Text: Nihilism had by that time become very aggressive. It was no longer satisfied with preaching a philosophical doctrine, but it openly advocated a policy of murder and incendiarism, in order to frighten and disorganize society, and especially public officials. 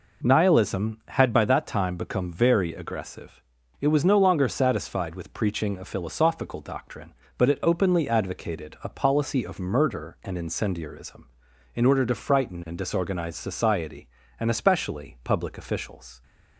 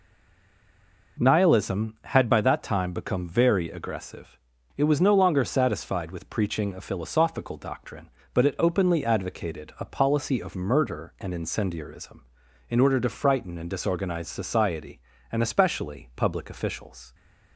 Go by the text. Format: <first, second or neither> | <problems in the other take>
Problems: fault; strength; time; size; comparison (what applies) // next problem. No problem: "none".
first | stays silent before the first word; until 1.1 s; 1.1 s long